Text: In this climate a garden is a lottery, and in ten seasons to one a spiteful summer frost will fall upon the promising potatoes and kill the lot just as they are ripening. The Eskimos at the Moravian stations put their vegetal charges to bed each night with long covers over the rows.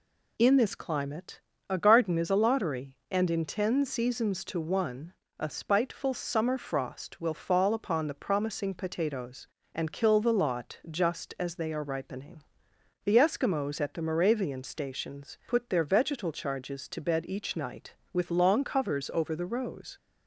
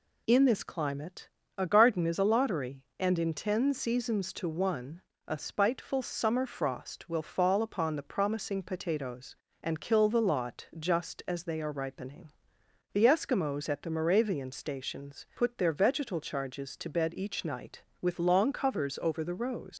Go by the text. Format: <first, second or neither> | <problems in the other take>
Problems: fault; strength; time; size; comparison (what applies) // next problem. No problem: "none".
first | pauses between "climate" and "a"; slight; at 1.2 s; 0.26 s long; slight in the first // pauses between "one" and "a"; slight; at 5.0 s; 0.24 s long; slight in the first // leaves "rows" unfinished; at 19.7 s; 75 ms